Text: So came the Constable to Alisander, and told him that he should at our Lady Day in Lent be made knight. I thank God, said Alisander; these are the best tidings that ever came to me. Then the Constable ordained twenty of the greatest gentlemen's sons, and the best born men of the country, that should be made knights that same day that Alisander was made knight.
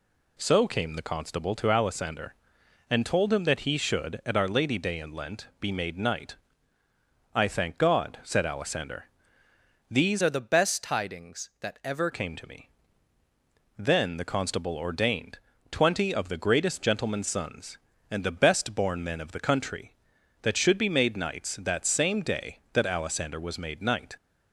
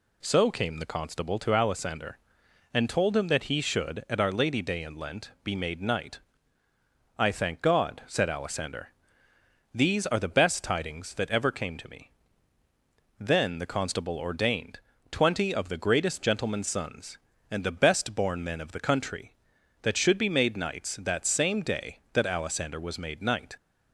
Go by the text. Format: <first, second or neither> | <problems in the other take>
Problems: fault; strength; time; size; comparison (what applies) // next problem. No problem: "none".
second | changes voice from "are" to "ever"; from 10.2 to 12.0 s; 1.8 s long // pauses between "ordained" and "twenty"; slight; at 15.3 s; 0.32 s long; slight in the second